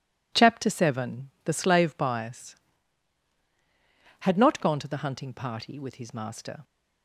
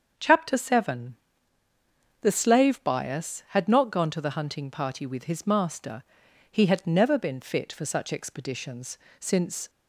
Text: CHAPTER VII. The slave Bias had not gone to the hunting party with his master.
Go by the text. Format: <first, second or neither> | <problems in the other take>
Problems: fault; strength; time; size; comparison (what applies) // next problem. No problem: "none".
first | starts louder than the rest; until 2.2 s; 7 dB // goes on to say "He had never been fit for such expeditions since"; strong; from 6.4 s on; 3.2 s long